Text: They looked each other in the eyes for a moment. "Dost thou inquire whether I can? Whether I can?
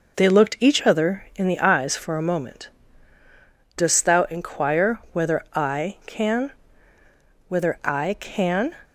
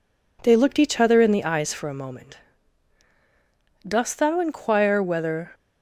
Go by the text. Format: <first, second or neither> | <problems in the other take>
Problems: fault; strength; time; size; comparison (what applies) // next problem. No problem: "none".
first | stops before "I can Whether I can"; at 5.5 s